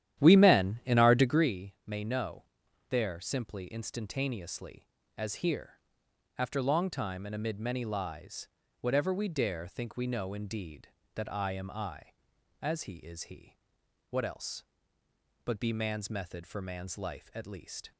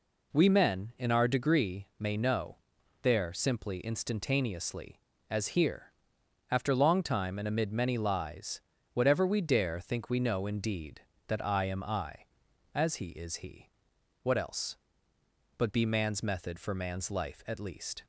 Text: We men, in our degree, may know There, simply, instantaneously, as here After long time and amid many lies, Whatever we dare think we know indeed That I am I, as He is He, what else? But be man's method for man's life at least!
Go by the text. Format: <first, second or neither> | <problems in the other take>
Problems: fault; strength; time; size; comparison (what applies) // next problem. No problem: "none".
second | starts louder than the rest; strong; until 1.5 s; 11.5 dB // pauses between "know" and "There"; noticeable; at 2.4 s; 0.46 s long; noticeable in the second // pauses between "here" and "After"; noticeable; at 5.7 s; 0.60 s long; noticeable in the second